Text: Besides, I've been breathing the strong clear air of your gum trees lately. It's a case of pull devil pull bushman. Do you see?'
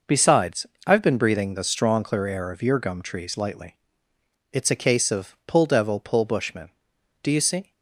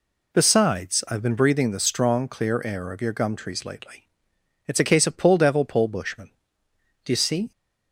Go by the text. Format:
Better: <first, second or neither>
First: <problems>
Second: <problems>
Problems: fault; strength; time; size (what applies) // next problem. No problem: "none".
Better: second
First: says "lightly" for "lately"; at 3.3 s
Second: none